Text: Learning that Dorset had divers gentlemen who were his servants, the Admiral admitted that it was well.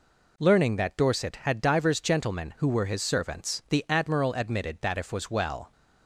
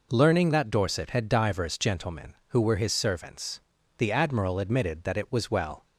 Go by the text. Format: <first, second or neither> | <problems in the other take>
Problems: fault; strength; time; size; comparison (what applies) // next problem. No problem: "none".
second | says "if" for "it"; at 4.9 s